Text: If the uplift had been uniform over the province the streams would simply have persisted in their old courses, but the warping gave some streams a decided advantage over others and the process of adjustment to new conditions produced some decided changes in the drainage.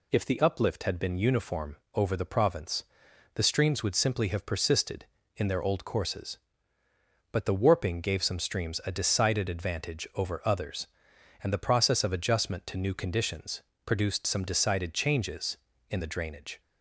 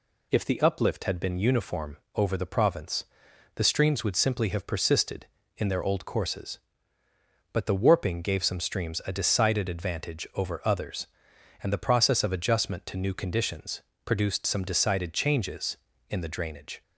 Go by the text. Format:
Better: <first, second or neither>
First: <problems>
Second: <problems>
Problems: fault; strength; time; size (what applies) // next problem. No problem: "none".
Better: neither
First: pauses between "uniform" and "over"; slight; at 1.7 s; 0.18 s long // pauses between "province" and "the"; noticeable; at 2.8 s; 0.50 s long // pauses between "conditions" and "produced"; slight; at 13.6 s; 0.22 s long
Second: pauses between "uniform" and "over"; slight; at 1.9 s; 0.18 s long // pauses between "province" and "the"; noticeable; at 3.0 s; 0.50 s long // pauses between "conditions" and "produced"; slight; at 13.8 s; 0.22 s long